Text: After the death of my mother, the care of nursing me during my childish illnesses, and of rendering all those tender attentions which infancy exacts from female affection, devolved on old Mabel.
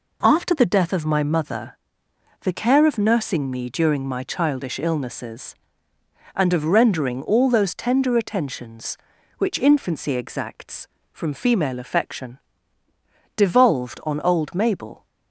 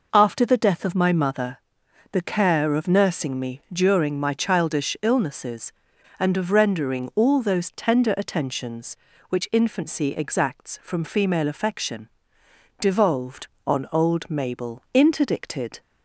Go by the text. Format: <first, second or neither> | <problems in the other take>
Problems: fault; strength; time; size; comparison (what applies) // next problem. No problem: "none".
first | goes on to say "Interdicted"; noticeable; from 14.9 s on; 0.88 s long